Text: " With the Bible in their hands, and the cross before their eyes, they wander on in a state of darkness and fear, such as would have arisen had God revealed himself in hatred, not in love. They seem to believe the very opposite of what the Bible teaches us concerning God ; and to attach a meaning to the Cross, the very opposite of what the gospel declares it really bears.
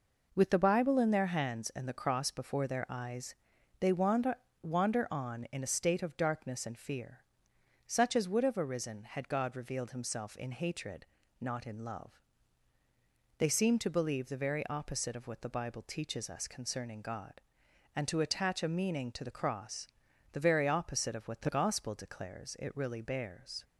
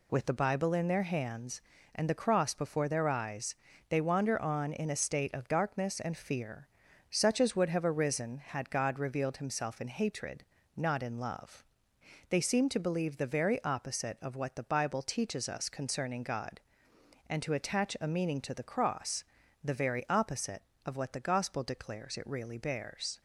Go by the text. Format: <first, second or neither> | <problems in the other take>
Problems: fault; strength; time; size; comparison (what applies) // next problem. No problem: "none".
second | says "wander" twice; at 4.6 s